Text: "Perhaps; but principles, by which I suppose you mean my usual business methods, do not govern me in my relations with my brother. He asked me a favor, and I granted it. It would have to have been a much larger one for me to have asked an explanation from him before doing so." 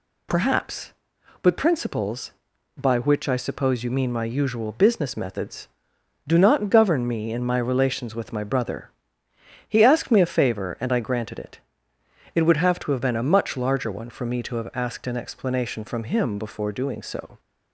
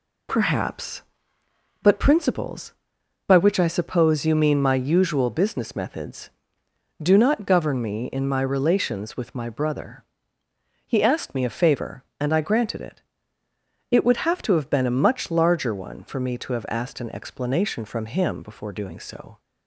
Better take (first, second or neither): neither